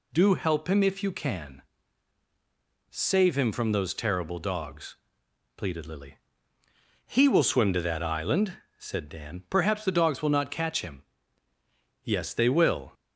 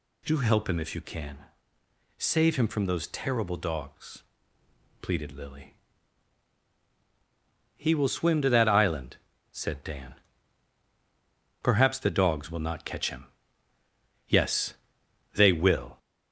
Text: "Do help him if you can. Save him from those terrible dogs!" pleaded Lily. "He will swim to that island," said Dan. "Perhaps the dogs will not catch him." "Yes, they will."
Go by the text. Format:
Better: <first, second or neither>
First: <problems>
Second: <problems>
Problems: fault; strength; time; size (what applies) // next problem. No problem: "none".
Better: first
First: none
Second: gets louder; throughout; 3.5 dB